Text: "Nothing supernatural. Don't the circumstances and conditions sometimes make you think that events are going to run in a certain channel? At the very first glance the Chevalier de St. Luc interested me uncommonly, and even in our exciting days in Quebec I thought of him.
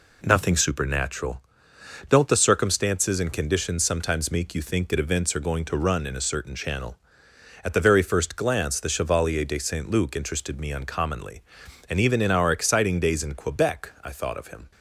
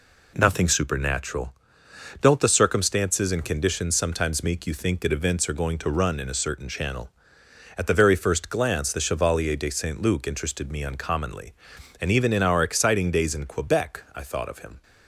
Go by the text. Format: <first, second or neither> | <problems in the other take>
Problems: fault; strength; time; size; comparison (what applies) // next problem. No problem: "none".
neither | none